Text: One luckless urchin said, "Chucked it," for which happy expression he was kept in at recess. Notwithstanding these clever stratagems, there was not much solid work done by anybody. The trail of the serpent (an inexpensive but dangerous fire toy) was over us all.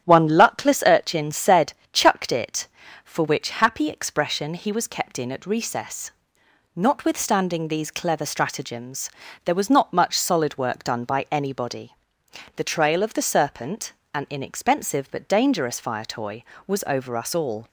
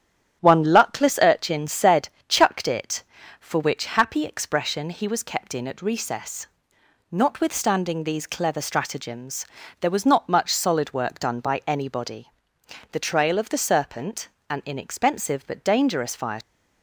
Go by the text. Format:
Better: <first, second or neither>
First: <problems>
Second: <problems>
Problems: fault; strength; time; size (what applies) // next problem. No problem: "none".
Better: first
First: starts louder than the rest; strong; until 1.0 s; 10.5 dB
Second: starts louder than the rest; strong; until 1.4 s; 10.5 dB // stops before "toy was over us all"; at 16.4 s